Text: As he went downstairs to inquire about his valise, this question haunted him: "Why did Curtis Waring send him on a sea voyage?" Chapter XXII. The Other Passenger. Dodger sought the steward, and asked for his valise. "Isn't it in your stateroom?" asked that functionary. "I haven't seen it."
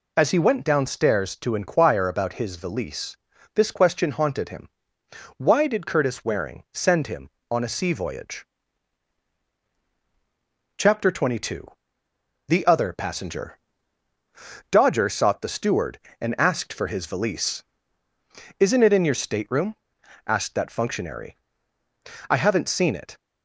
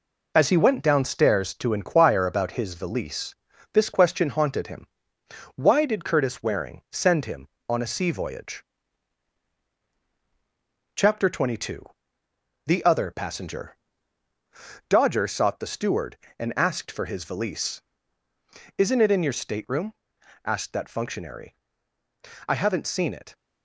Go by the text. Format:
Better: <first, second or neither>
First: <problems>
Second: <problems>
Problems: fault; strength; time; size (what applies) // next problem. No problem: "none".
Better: first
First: none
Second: gets quieter; noticeable; throughout; 5.5 dB